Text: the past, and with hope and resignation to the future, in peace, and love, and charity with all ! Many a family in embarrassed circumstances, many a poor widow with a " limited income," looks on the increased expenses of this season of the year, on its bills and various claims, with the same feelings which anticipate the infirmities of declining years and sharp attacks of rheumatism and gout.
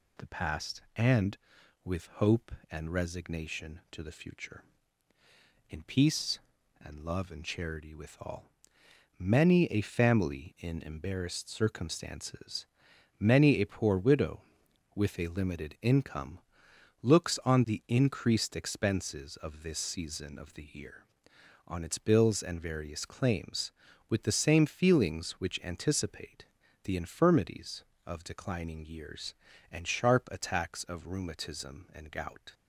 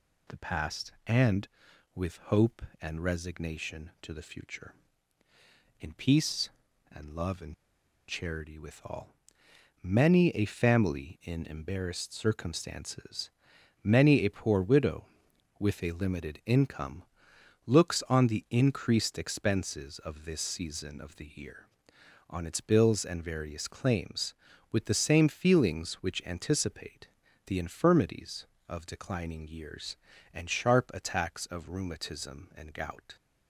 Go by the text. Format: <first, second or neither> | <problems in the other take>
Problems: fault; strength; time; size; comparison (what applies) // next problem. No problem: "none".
first | pauses between "and" and "charity"; noticeable; at 7.5 s; 0.54 s long // pauses between "anticipate" and "the"; at 27.0 s; 0.38 s long; also in the first